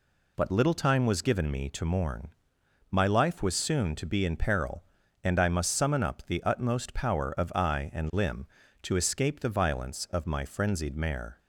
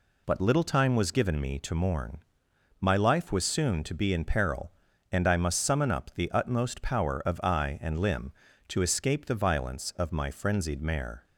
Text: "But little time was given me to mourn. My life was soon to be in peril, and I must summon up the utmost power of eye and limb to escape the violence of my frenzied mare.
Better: neither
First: none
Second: none

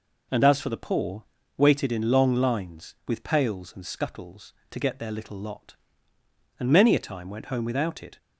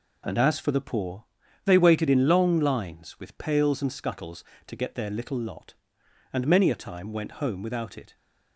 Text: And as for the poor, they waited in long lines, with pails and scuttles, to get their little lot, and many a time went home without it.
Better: second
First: skips "they"; at 1.3 s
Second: none

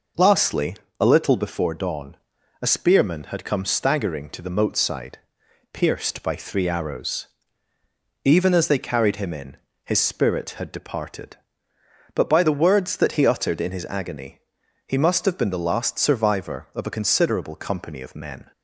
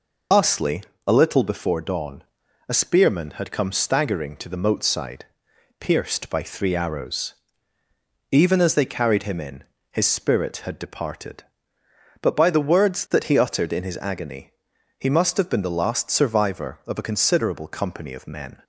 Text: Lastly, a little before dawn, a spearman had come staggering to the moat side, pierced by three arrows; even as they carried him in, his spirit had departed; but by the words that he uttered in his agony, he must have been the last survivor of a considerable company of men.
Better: first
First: none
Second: loses the start of "Lastly"; at 0.3 s; 70 ms

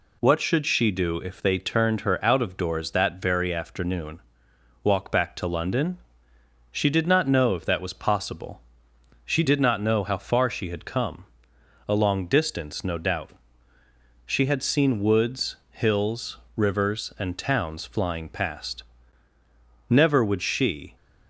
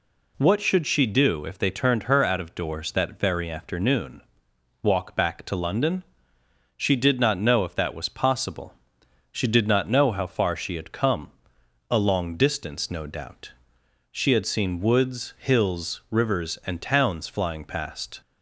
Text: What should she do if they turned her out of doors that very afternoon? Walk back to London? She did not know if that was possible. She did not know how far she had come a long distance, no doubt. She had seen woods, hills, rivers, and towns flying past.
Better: second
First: pauses between "come" and "a"; noticeable; at 11.2 s; 0.64 s long // goes on to say "Never would she"; noticeable; from 19.8 s on; 1.0 s long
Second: pauses between "come" and "a"; noticeable; at 11.2 s; 0.60 s long

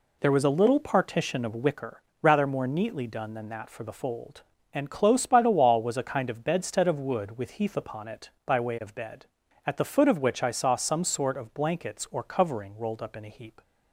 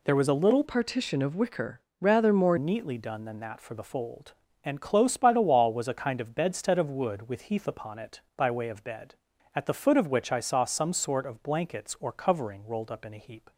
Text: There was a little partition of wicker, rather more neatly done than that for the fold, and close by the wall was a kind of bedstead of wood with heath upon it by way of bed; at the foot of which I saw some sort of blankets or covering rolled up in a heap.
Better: first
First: none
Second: changes voice from "partition" to "more"; from 0.6 to 2.5 s; 1.9 s long

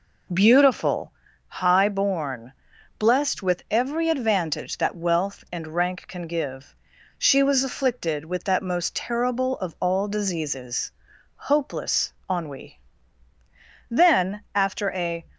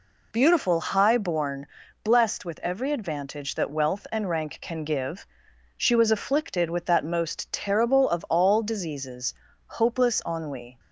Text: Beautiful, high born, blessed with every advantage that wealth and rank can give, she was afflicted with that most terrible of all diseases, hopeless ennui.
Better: second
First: pauses between "hopeless" and "ennui"; slight; at 12.1 s; 0.16 s long // goes on to say "Then after a"; from 13.8 s on; 1.3 s long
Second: none

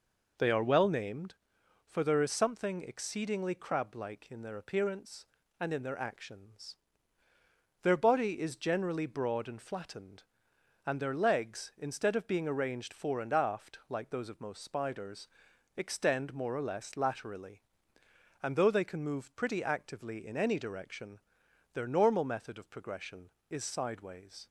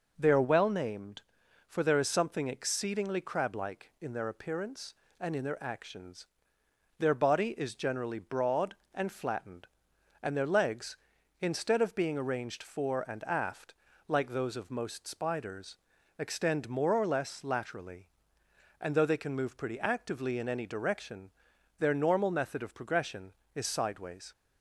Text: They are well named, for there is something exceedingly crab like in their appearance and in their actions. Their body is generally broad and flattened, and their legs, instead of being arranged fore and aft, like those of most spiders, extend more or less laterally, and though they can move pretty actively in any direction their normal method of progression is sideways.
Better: neither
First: pauses between "direction" and "their"; noticeable; at 21.1 s; 0.54 s long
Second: pauses between "direction" and "their"; noticeable; at 21.2 s; 0.48 s long

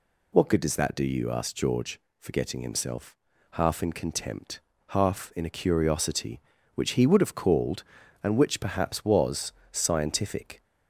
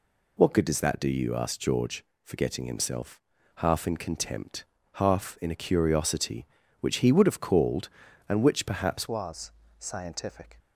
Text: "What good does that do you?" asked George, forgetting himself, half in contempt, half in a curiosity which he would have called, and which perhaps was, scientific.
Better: first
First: none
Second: changes voice at "was"; from 9.0 s on; 1.5 s long

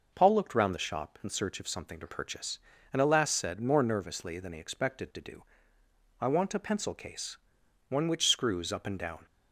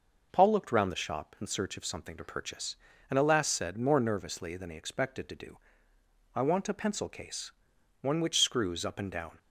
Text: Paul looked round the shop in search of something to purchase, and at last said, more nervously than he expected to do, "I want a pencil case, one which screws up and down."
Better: neither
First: none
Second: none

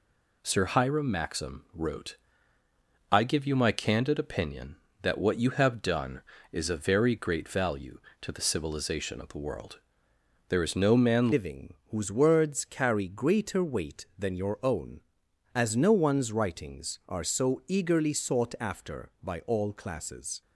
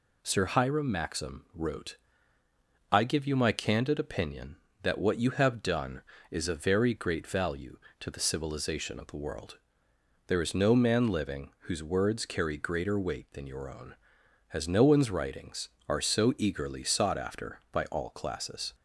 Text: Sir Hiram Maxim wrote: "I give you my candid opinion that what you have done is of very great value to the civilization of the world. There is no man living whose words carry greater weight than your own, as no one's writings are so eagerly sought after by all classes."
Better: second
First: changes voice at "living"; from 11.3 s on; 9.1 s long // pauses between "living" and "whose"; slight; at 11.7 s; 0.16 s long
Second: none

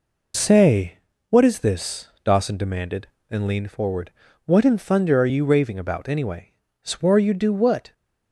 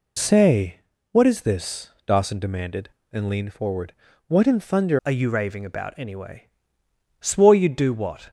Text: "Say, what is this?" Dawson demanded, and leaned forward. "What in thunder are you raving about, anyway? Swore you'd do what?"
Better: first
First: none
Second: changes voice at "are"; from 5.0 s on; 3.2 s long

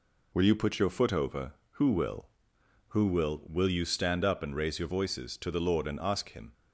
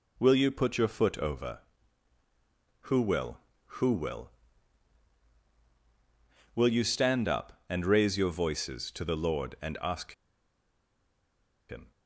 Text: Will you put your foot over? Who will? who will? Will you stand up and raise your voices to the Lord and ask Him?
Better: first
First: none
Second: pauses between "ask" and "Him"; strong; at 10.1 s; 1.5 s long

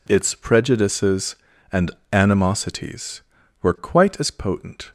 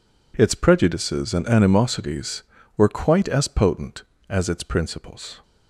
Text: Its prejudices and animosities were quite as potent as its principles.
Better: second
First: pauses between "and" and "animosities"; slight; at 1.9 s; 0.22 s long // stops before "as its principles"; at 4.8 s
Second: none

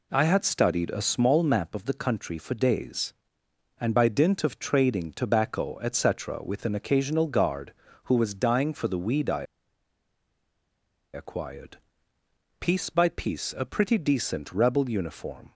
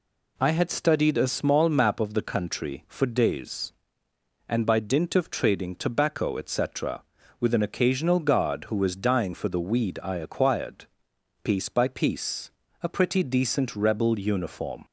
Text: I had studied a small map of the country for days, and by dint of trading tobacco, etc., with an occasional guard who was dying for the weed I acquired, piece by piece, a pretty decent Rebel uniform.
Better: second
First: pauses between "I" and "acquired"; strong; at 9.4 s; 1.7 s long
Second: none

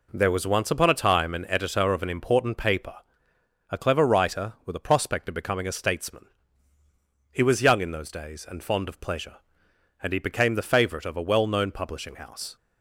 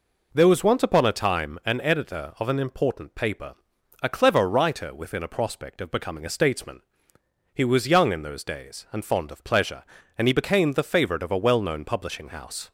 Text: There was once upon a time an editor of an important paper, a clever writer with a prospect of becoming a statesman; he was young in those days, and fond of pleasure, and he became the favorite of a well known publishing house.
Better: first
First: none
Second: says "within" for "with"; at 4.9 s

